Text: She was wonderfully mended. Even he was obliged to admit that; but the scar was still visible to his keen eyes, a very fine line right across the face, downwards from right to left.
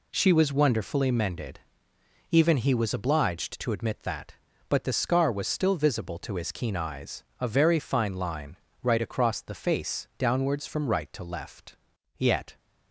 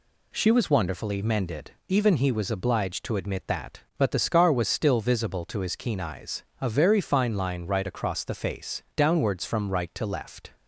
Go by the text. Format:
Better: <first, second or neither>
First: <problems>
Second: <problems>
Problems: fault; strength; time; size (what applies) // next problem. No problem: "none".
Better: second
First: pauses between "line" and "right"; slight; at 8.5 s; 0.26 s long // goes on to say "Yet"; slight; from 12.1 s on; 0.40 s long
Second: none